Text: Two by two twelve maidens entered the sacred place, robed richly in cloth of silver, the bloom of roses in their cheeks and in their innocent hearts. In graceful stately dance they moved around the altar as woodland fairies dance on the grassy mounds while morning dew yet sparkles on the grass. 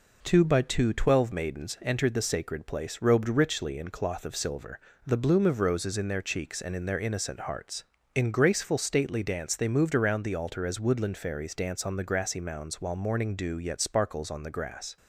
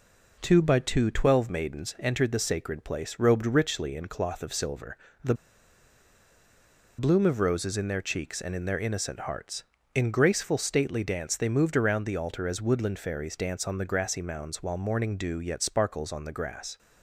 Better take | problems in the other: first | pauses between "the" and "bloom"; strong; at 5.3 s; 1.6 s long

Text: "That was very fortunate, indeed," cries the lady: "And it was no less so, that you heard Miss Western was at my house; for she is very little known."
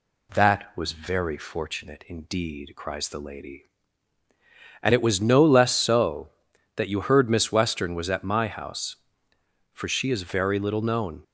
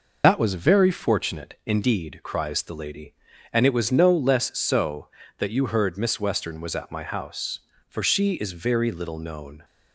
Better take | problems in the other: first | loses the start of "That"; at 0.2 s; 100 ms

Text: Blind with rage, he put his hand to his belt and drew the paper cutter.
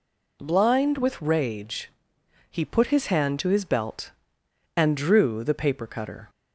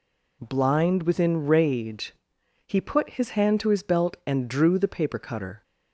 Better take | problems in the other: first | says "within" for "with"; at 1.0 s

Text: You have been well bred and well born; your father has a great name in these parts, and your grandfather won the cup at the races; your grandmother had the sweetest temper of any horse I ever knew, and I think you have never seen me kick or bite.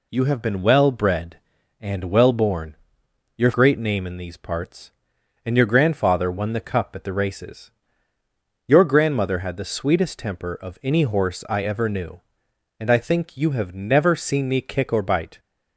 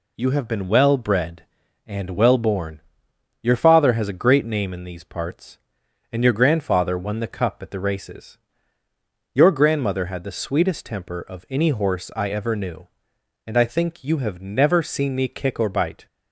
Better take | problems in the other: second | skips "father has a"; at 3.5 s

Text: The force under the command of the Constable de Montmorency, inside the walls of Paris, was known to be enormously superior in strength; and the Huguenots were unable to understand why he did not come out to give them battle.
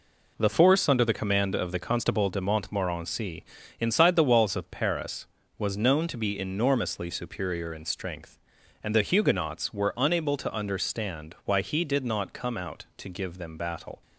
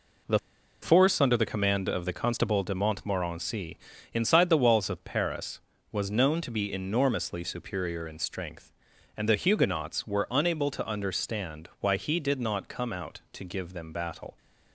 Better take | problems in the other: first | pauses between "The" and "force"; at 0.3 s; 0.43 s long

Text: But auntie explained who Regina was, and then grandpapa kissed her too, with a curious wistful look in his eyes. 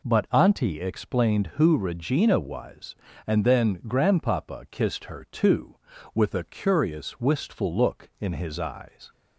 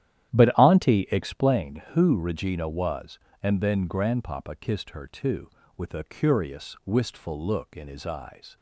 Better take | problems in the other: first | starts louder than the rest; strong; until 1.5 s; 12 dB

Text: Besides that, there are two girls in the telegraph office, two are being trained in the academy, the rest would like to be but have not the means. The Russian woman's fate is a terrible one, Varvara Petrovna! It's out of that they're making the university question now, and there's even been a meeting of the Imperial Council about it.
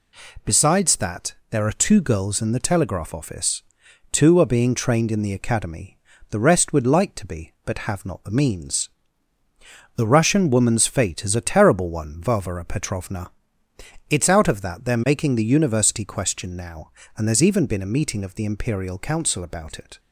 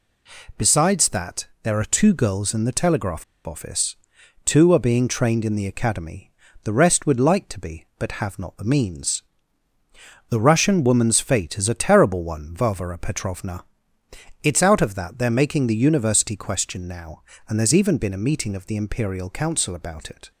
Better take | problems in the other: first | pauses between "telegraph" and "office"; slight; at 3.2 s; 0.22 s long

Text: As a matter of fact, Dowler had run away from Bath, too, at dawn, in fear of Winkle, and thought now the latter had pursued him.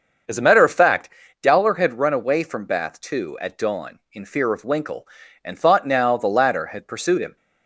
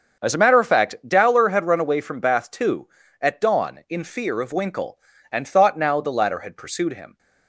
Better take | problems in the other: neither | starts louder than the rest; the same in both

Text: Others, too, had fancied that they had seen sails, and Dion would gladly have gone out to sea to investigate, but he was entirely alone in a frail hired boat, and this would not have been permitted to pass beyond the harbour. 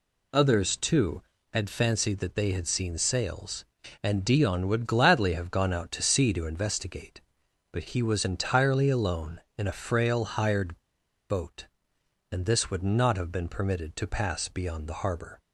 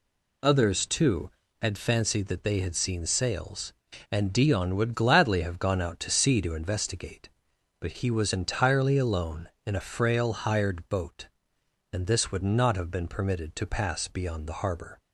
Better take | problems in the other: second | pauses between "hired" and "boat"; noticeable; at 10.7 s; 0.50 s long

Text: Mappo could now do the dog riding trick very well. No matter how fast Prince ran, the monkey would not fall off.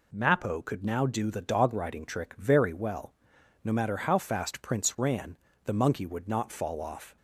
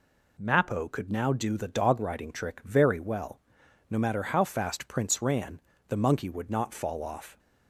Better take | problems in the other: neither | none

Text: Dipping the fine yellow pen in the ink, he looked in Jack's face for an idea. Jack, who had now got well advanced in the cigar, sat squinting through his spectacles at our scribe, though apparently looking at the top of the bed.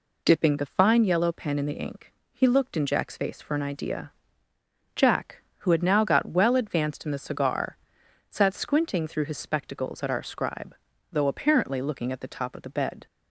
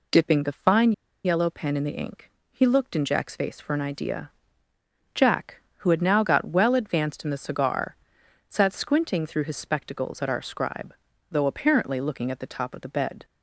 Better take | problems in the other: first | pauses between "fine" and "yellow"; slight; at 0.9 s; 0.34 s long

